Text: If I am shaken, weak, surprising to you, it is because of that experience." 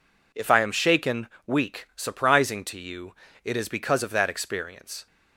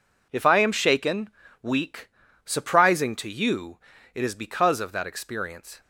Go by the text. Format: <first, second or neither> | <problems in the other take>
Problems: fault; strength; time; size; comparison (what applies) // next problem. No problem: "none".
neither | none